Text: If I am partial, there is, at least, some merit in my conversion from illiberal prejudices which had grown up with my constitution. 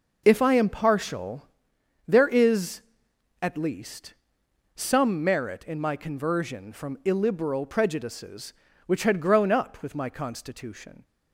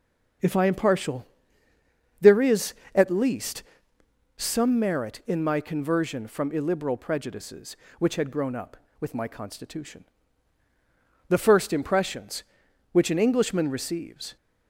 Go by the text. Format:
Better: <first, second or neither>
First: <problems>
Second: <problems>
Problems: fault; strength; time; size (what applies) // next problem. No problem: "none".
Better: first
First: none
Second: starts louder than the rest; until 2.3 s; 6.5 dB // goes on to say "The first impressions which an Englishman receives"; strong; from 11.2 s on; 3.0 s long